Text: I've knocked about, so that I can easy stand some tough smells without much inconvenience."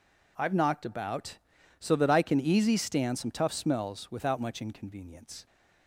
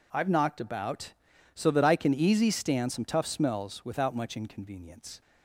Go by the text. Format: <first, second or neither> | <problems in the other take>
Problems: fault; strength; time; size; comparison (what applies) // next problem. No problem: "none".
neither | none